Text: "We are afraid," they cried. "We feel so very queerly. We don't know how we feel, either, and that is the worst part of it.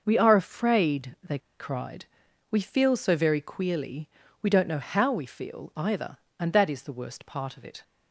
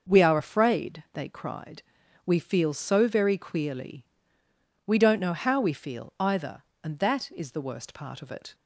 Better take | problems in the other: second | starts louder than the rest; until 1.0 s; 6 dB; also in the second // pauses between "they" and "cried"; slight; at 1.3 s; 0.21 s long

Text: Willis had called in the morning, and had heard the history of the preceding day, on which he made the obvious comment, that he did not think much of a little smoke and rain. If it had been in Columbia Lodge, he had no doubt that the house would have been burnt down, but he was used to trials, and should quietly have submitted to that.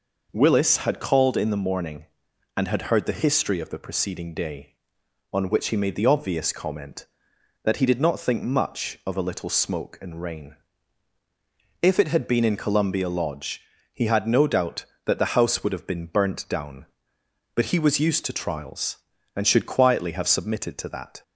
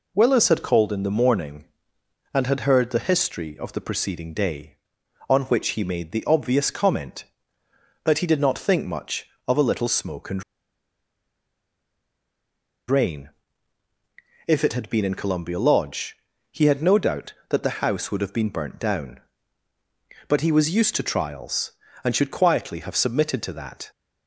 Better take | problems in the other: first | pauses between "and" and "rain"; strong; at 10.4 s; 2.4 s long

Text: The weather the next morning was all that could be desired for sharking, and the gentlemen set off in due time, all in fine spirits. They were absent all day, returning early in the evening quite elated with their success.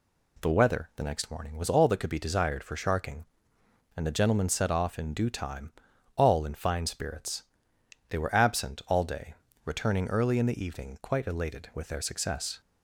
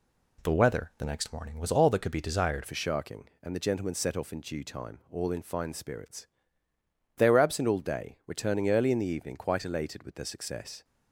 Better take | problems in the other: first | changes voice at "for"; from 2.6 s on; 8.2 s long

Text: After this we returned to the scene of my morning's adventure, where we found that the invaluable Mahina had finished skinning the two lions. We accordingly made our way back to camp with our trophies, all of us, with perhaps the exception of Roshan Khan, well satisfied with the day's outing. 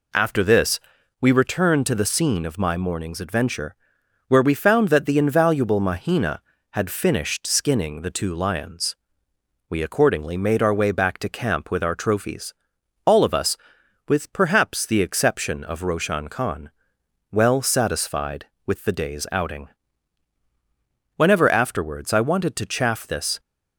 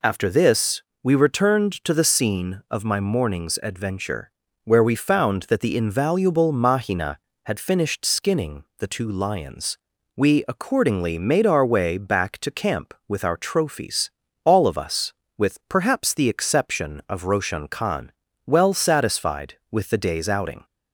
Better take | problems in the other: second | pauses between "this" and "we"; at 0.7 s; 0.40 s long; slight in the second // goes on to say "Whenever afterwards I wanted to chaff this"; strong; from 21.1 s on; 2.2 s long

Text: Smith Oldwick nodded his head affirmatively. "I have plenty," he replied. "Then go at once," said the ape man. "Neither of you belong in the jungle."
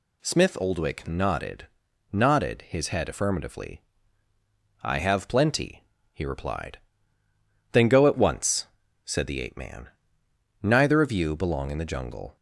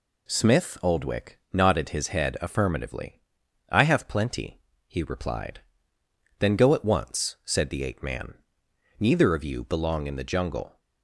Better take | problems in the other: second | says "nodded" twice; at 2.1 s

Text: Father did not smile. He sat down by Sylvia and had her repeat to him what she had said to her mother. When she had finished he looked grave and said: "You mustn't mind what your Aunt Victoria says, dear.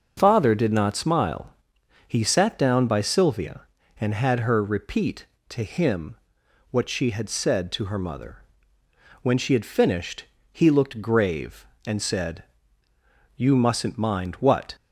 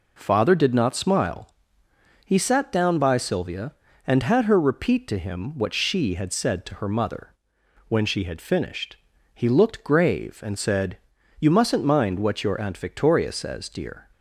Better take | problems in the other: second | starts louder than the rest; until 1.1 s; 6.5 dB // pauses between "him" and "what"; noticeable; at 6.1 s; 0.56 s long // pauses between "finished" and "he"; slight; at 10.2 s; 0.28 s long; also in the second // stops before "your Aunt Victoria says dear"; at 14.7 s

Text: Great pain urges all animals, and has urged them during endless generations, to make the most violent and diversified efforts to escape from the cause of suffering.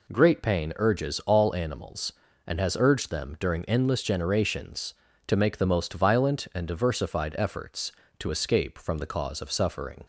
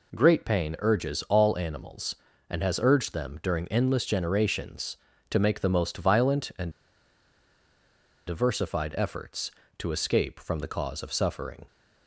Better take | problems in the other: first | pauses between "and" and "diversified"; strong; at 6.7 s; 1.5 s long

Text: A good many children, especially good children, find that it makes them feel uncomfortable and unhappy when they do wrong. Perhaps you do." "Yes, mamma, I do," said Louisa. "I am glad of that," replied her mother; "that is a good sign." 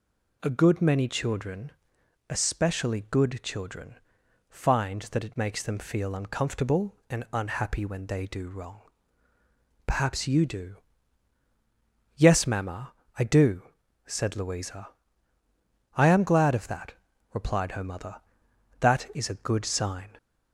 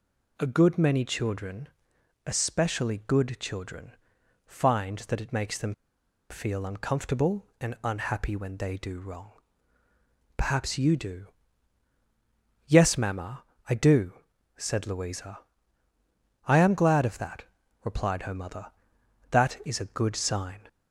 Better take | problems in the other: first | pauses between "them" and "feel"; noticeable; at 5.7 s; 0.57 s long

